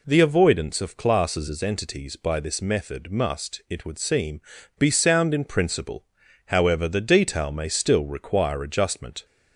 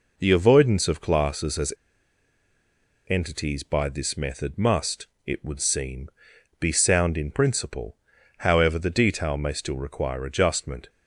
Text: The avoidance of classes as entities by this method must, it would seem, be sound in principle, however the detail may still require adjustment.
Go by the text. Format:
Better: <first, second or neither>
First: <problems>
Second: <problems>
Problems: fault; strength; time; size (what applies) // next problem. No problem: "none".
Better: first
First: none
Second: pauses between "as" and "entities"; strong; at 1.7 s; 1.3 s long